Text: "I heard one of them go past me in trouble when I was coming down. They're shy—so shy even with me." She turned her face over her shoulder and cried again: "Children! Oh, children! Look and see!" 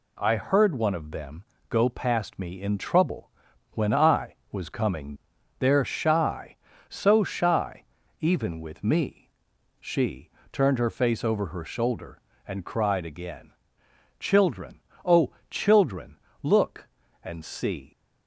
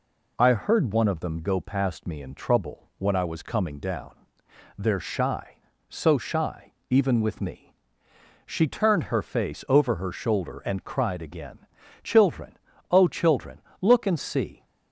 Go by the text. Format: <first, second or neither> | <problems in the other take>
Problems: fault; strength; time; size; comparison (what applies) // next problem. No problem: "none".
second | pauses between "them" and "go"; slight; at 1.4 s; 0.26 s long // pauses between "trouble" and "when"; at 3.2 s; 0.44 s long // skips "down"; at 5.3 s // pauses between "shy" and "even"; at 7.8 s; 0.38 s long; slight in the second // pauses between "She" and "turned"; slight; at 10.2 s; 0.24 s long